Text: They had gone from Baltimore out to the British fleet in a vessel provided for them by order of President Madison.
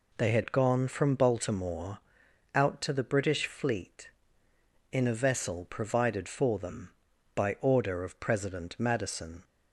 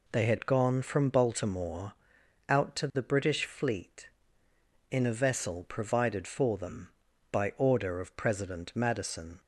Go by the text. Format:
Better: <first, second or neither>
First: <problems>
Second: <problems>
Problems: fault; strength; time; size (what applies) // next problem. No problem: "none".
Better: neither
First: pauses between "Baltimore" and "out"; noticeable; at 1.9 s; 0.56 s long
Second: pauses between "Baltimore" and "out"; noticeable; at 1.9 s; 0.56 s long